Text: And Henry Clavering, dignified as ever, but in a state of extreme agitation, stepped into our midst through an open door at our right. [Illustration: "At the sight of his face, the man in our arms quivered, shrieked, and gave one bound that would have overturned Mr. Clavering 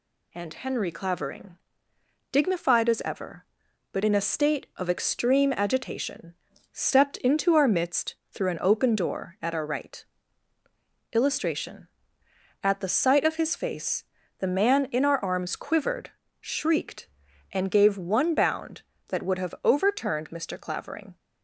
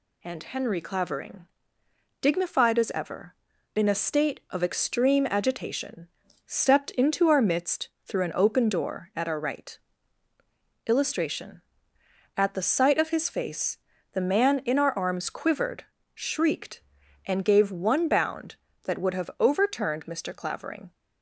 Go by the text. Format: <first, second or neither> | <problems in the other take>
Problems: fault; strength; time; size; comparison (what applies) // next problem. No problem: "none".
first | skips "but"; at 3.5 s // pauses between "midst" and "through"; slight; at 7.8 s; 0.18 s long; slight in the first